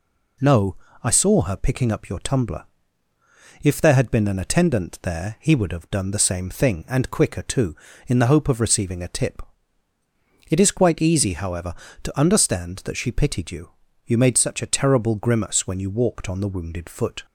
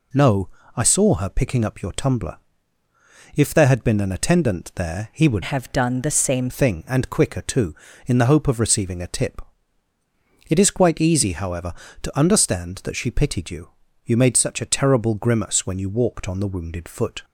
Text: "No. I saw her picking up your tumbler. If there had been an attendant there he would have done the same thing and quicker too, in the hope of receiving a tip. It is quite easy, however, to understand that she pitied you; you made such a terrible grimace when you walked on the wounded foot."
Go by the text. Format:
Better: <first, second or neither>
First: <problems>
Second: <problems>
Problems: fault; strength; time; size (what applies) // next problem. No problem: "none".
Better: first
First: none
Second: changes voice from "have" to "same"; from 5.4 to 6.5 s; 1.1 s long